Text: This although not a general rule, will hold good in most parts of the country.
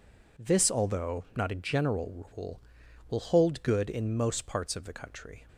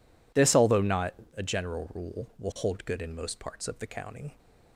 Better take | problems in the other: first | pauses between "not" and "a"; slight; at 1.1 s; 0.22 s long // says "county" for "country"; at 3.8 s

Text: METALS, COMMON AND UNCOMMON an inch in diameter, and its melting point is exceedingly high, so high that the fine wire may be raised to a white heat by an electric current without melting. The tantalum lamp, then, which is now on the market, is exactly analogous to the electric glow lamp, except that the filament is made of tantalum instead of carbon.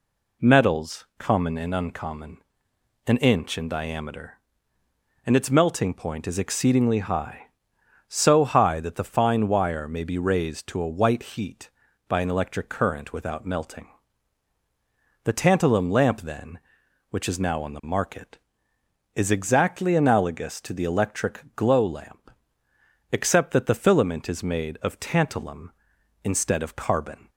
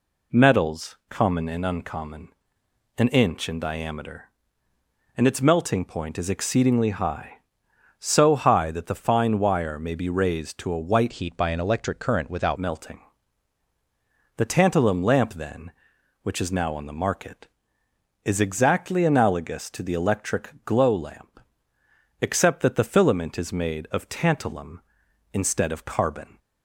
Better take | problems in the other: first | pauses between "UNCOMMON" and "an"; noticeable; at 2.2 s; 0.70 s long; noticeable in the first // changes voice from "heat" to "without"; from 11.1 to 12.5 s; 1.4 s long

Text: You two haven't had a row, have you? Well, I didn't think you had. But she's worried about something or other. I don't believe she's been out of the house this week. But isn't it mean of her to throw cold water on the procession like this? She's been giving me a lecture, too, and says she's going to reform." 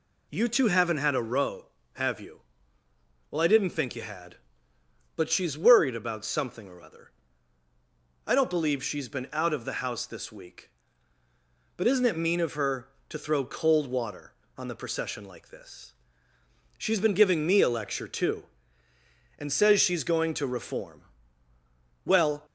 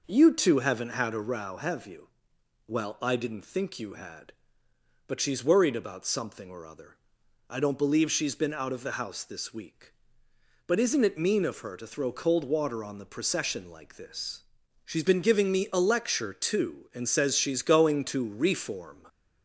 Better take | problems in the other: second | goes on to say "Well"; slight; from 22.0 s on; 0.40 s long

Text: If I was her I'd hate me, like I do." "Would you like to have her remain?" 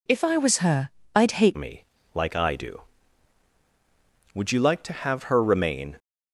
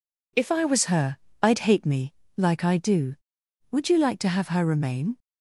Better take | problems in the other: second | pauses between "her" and "I'd"; slight; at 0.8 s; 0.26 s long; slight in the second // changes voice at "me"; from 1.5 s on; 4.4 s long

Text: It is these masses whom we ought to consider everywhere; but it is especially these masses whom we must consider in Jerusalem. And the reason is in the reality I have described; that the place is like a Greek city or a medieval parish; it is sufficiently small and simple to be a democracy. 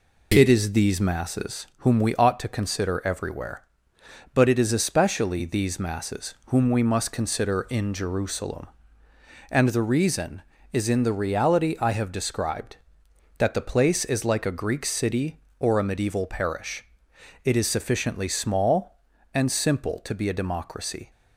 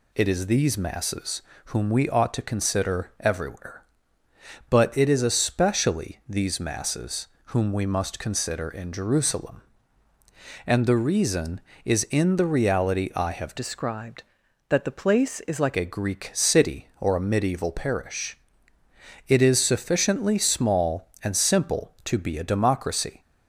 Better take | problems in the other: first | pauses between "masses" and "whom"; slight; at 1.4 s; 0.26 s long // pauses between "masses" and "whom"; slight; at 7.2 s; 0.18 s long // changes voice from "described" to "like"; from 13.5 to 15.7 s; 2.2 s long

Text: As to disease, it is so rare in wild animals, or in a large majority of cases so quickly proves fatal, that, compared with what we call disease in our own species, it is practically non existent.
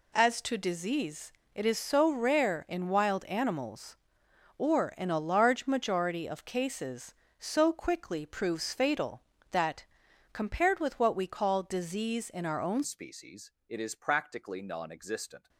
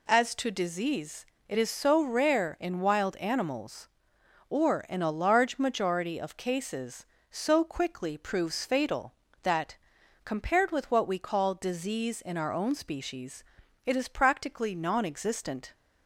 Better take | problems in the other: second | changes voice at "species"; from 12.8 s on; 2.6 s long

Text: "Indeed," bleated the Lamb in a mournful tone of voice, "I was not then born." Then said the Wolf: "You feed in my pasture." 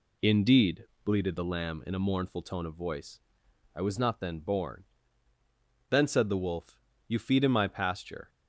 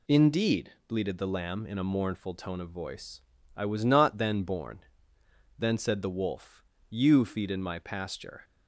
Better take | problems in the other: neither | none

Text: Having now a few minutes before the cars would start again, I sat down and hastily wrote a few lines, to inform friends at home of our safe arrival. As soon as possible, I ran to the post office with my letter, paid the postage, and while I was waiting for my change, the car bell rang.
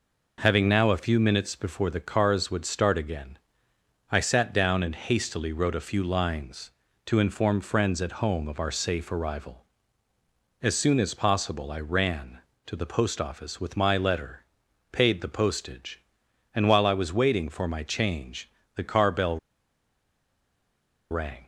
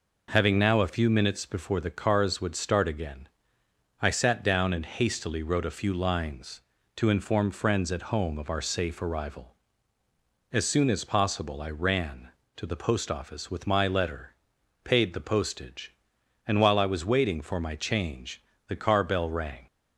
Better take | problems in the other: second | pauses between "bell" and "rang"; strong; at 19.3 s; 1.7 s long

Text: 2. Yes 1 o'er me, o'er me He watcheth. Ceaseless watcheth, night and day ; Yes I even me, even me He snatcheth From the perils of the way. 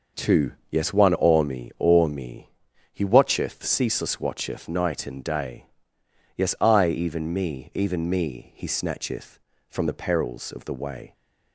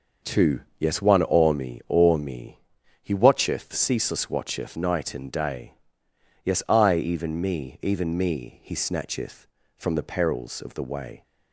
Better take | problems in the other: neither | pauses between "me" and "He"; the same in both

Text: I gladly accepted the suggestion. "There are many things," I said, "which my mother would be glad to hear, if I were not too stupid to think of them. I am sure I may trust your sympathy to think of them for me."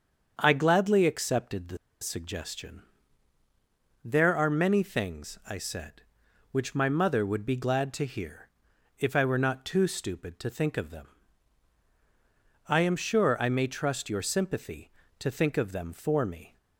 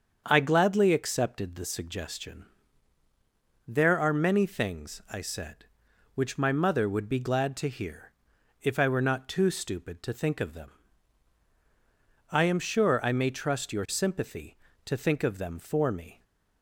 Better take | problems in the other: second | starts louder than the rest; strong; until 1.3 s; 7 dB; strong in the second // pauses between "the" and "suggestion"; slight; at 1.7 s; 0.25 s long

